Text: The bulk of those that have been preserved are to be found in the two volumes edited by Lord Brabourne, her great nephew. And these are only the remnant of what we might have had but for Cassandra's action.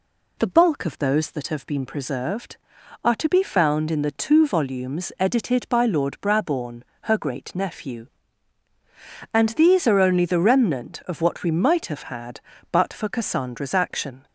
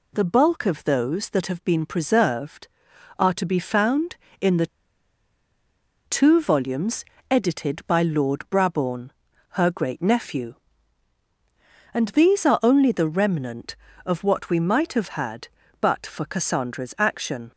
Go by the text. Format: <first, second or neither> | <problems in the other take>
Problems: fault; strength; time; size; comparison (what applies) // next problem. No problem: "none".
first | pauses between "the" and "two"; strong; at 4.6 s; 1.4 s long // pauses between "volumes" and "edited"; slight; at 7.0 s; 0.26 s long